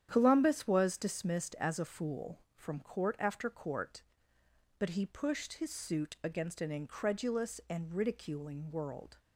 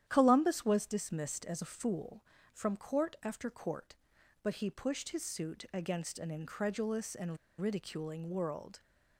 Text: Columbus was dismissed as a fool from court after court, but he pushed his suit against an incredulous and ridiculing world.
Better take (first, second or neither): first